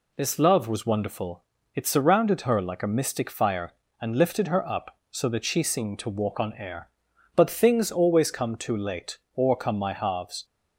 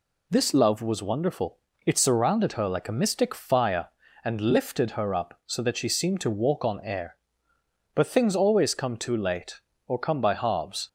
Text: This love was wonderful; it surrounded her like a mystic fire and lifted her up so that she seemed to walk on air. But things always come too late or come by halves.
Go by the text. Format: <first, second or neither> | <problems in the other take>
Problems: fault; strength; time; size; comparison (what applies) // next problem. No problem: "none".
second | says "my" for "by"; at 9.7 s